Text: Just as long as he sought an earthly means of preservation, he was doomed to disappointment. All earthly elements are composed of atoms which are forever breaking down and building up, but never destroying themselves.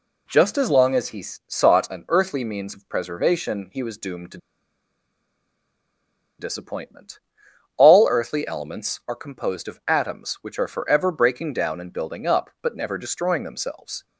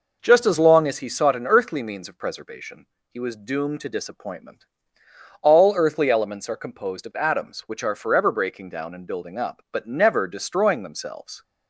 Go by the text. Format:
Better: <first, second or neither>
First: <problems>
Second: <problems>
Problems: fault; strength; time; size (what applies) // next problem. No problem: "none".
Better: second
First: pauses between "he" and "sought"; slight; at 1.2 s; 0.24 s long // pauses between "to" and "disappointment"; strong; at 4.3 s; 2.0 s long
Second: none